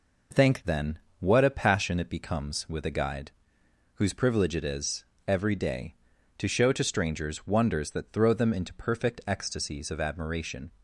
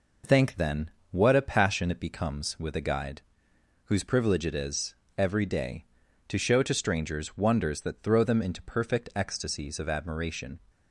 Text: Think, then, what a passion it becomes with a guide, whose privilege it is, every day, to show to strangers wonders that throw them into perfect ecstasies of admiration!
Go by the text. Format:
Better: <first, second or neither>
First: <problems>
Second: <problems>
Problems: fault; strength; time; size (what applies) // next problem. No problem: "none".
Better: neither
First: none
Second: none